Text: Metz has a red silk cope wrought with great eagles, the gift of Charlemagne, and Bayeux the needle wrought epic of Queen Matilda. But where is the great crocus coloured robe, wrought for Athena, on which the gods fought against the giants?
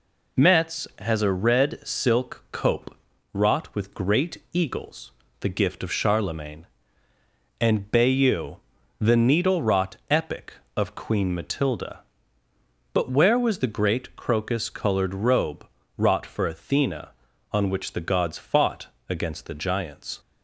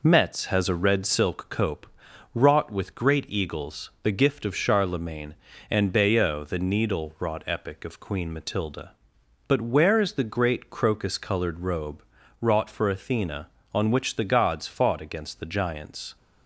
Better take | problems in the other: second | pauses between "cope" and "wrought"; at 2.9 s; 0.40 s long; noticeable in the second // pauses between "Bayeux" and "the"; at 8.5 s; 0.42 s long // pauses between "wrought" and "epic"; slight; at 9.9 s; 0.16 s long // says "was" for "is"; at 13.3 s // pauses between "fought" and "against"; slight; at 18.8 s; 0.22 s long

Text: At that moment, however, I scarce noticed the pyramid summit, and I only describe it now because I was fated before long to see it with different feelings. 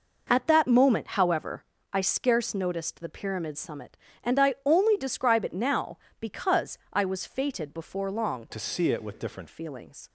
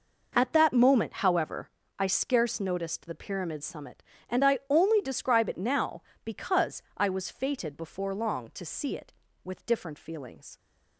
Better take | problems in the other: second | pauses between "because" and "I"; slight; at 6.7 s; 0.16 s long; slight in the second // changes voice from "to" to "different"; from 8.4 to 9.4 s; 1.0 s long

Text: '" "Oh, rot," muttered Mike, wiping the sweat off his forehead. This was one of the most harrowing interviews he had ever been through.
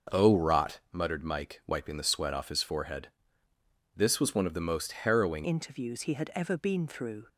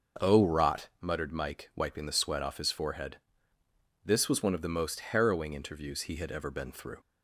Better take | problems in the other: second | starts louder than the rest; noticeable; until 1.2 s; 6 dB; also in the second // changes voice at "interviews"; from 5.4 s on; 1.8 s long

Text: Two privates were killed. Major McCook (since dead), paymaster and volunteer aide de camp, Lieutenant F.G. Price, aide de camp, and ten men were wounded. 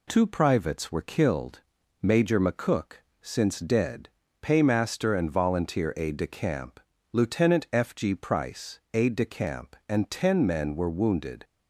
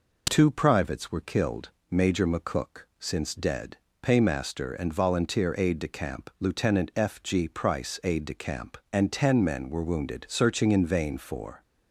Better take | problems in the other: first | goes on to say "Searching in vain for"; from 10.3 s on; 1.3 s long

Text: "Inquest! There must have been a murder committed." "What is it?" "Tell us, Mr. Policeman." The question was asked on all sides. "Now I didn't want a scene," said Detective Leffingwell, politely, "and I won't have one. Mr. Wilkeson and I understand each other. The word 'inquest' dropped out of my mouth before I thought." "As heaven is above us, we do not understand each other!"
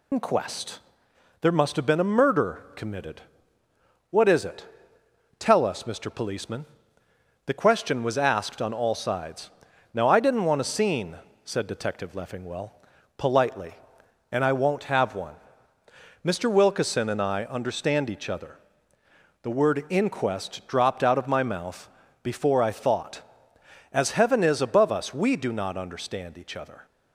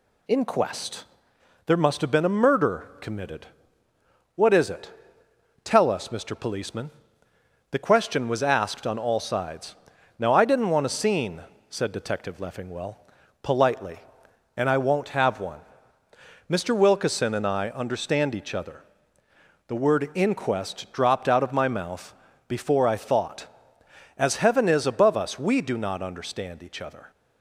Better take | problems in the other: second | loses the start of "Inquest"; at 0.1 s; 90 ms // pauses between "mouth" and "before"; slight; at 21.8 s; 0.34 s long; slight in the second

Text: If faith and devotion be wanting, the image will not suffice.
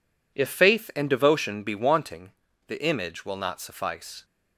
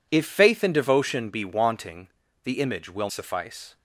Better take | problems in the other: first | skips "not"; at 3.0 s

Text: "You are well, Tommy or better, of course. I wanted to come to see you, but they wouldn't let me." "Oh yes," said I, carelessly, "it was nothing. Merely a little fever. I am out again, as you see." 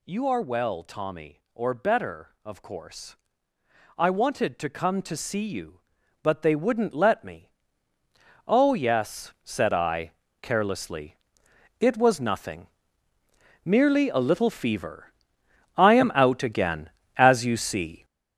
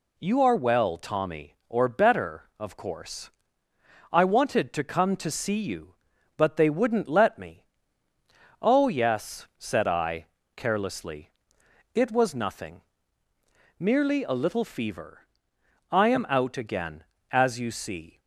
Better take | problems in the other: second | gets louder; strong; throughout; 8.5 dB

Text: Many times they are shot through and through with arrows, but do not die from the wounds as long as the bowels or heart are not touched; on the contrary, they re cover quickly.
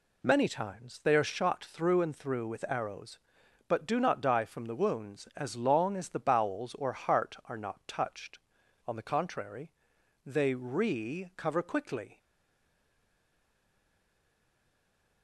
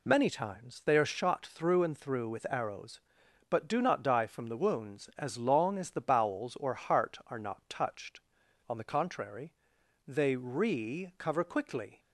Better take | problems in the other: second | stays silent after the last word; strong; from 12.1 s on; 3.1 s long

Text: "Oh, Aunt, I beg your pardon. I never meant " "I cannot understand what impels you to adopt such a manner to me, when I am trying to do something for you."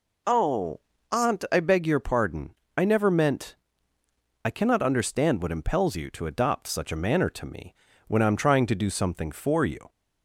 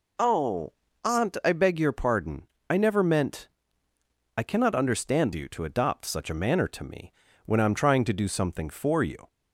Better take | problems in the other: first | skips "what impels"; at 5.3 s

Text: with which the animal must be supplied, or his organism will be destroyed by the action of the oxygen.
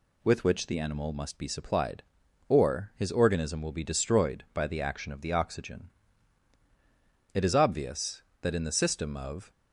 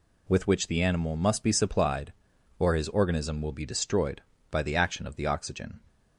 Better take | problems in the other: second | goes on to say "It is obvious that in the system of"; strong; from 7.3 s on; 2.1 s long

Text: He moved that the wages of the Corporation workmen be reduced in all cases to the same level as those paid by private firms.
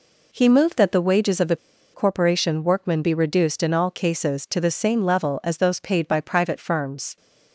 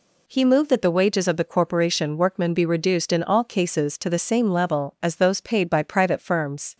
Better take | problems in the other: second | pauses between "the" and "Corporation"; at 1.5 s; 0.36 s long

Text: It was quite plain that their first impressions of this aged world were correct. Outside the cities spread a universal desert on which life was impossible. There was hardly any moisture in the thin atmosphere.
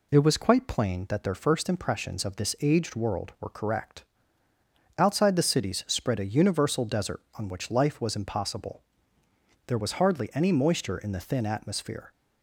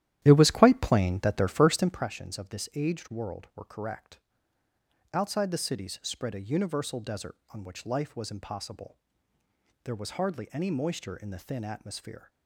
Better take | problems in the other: first | starts louder than the rest; strong; until 2.1 s; 12 dB

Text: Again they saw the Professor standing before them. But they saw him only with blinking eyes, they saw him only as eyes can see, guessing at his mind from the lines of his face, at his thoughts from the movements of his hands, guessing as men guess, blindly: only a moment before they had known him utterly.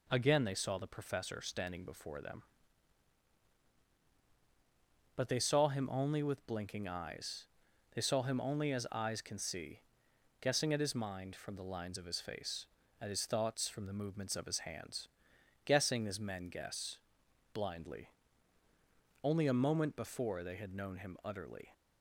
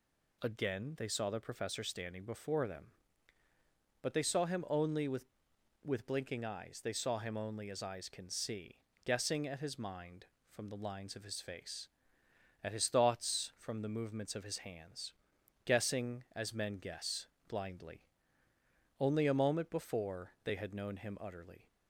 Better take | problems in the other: first | says "with" twice; at 5.8 s

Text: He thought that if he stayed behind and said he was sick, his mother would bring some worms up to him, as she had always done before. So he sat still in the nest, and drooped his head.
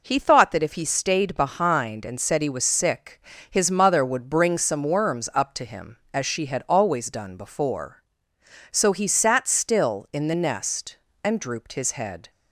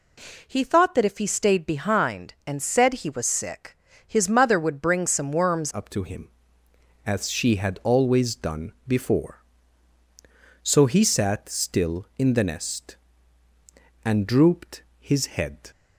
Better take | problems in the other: first | changes voice at "up"; from 5.7 s on; 10.0 s long // pauses between "done" and "before"; slight; at 8.7 s; 0.16 s long // pauses between "drooped" and "his"; slight; at 14.8 s; 0.16 s long

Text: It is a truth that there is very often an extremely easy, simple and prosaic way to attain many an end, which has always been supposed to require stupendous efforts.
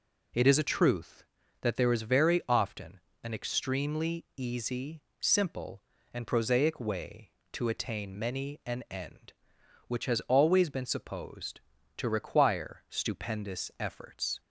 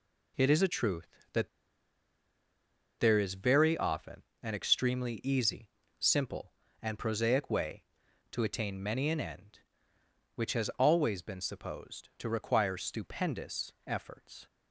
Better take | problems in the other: first | pauses between "that" and "there"; strong; at 1.4 s; 1.5 s long // pauses between "often" and "an"; slight; at 4.2 s; 0.20 s long; slight in the first

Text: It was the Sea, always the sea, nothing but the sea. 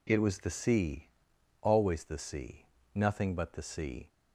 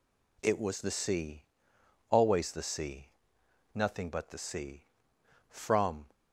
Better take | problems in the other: first | goes on to say "From"; from 5.4 s on; 0.60 s long

